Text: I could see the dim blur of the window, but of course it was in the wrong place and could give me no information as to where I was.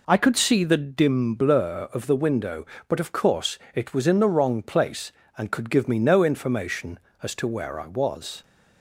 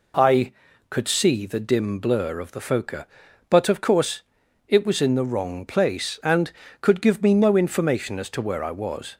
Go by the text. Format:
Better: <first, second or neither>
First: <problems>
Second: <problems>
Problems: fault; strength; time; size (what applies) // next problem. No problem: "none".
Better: first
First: pauses between "course" and "it"; slight; at 3.5 s; 0.16 s long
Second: says "phoca" for "window"; at 2.6 s // pauses between "course" and "it"; at 4.2 s; 0.44 s long